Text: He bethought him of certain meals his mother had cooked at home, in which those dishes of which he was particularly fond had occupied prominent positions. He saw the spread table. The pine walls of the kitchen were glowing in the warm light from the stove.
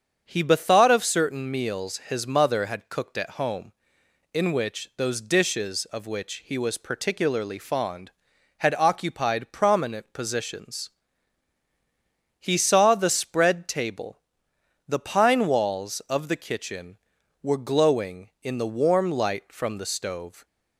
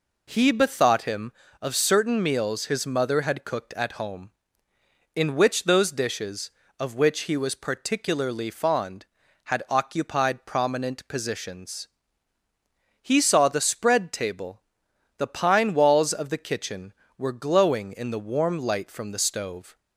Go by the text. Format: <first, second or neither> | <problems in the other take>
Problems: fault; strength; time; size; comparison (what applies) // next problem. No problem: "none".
second | starts louder than the rest; strong; until 1.2 s; 7.5 dB // skips "him"; at 0.8 s